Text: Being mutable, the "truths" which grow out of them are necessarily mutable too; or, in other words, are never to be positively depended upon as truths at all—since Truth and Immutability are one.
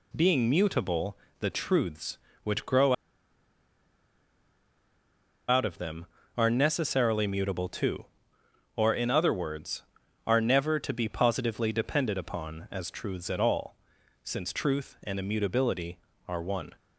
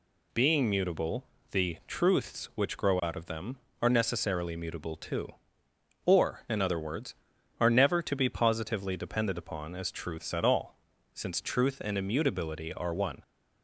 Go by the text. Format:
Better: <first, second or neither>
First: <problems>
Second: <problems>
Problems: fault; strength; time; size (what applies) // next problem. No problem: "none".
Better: second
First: pauses between "grow" and "out"; strong; at 2.9 s; 2.5 s long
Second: none